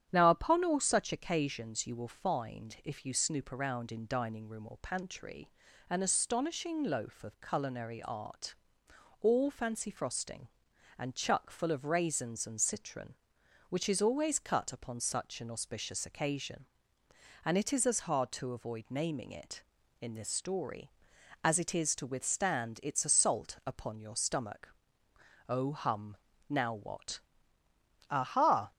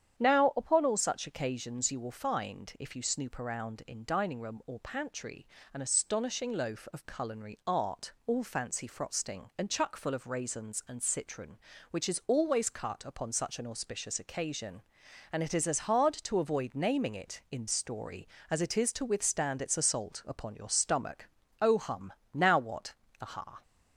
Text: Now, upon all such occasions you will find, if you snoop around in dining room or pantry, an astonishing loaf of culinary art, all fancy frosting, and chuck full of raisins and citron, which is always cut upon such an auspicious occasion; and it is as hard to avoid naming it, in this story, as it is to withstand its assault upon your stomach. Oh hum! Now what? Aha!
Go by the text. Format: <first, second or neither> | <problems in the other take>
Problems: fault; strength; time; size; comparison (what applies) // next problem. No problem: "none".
first | starts louder than the rest; strong; until 1.2 s; 9 dB; strong in the first // skips "this"; at 17.6 s